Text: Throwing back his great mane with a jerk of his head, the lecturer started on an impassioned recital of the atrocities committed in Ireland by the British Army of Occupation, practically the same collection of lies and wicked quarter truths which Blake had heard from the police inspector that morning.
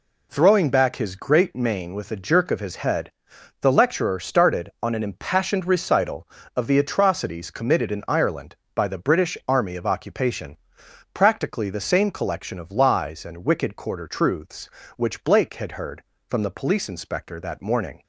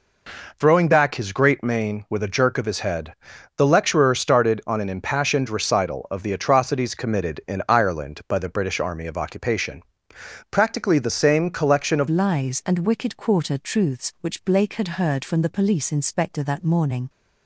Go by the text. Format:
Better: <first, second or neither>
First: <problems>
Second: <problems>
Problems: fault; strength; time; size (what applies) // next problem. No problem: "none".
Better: first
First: none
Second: changes voice at "lies"; from 12.0 s on; 5.0 s long